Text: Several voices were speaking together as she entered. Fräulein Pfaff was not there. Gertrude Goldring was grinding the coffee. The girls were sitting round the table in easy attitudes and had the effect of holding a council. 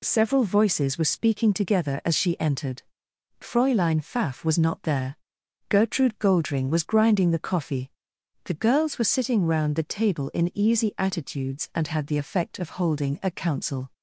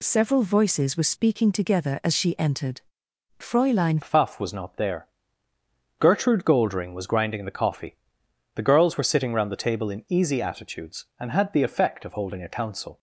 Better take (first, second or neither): first